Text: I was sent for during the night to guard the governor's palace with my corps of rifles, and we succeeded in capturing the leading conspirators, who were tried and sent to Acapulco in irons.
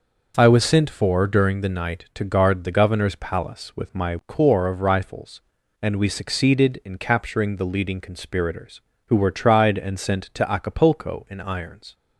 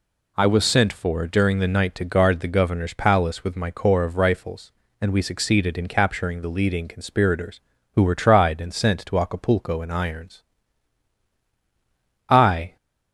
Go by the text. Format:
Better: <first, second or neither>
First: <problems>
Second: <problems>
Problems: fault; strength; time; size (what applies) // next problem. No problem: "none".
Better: first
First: none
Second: goes on to say "I"; slight; from 12.3 s on; 0.46 s long